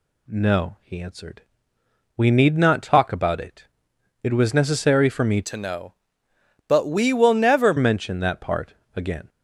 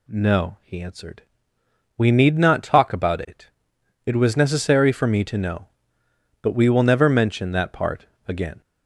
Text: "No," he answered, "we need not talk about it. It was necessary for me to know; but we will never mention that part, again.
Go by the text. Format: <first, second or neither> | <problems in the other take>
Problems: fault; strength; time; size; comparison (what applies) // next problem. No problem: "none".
second | changes voice from "to" to "never"; from 5.4 to 7.7 s; 2.3 s long